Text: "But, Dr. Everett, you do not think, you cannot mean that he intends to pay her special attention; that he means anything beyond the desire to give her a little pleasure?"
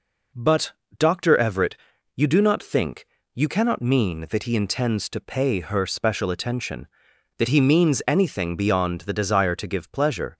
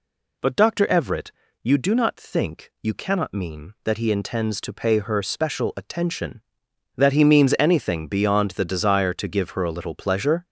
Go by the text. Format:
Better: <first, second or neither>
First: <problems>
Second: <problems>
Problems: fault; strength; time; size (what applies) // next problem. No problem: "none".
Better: second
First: skips "her a little"; at 9.9 s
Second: none